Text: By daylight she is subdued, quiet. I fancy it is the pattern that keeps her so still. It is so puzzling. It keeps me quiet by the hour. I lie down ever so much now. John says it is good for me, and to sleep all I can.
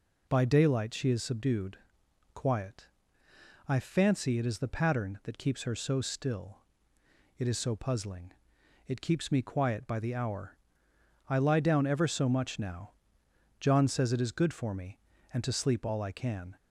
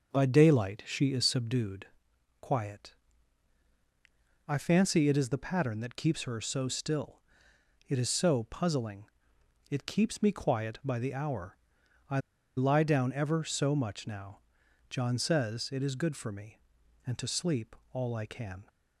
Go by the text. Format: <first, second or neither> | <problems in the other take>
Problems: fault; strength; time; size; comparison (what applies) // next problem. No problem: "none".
first | starts louder than the rest; until 1.1 s; 6 dB // pauses between "I" and "lie"; at 12.1 s; 0.37 s long // pauses between "sleep" and "all"; slight; at 17.7 s; 0.16 s long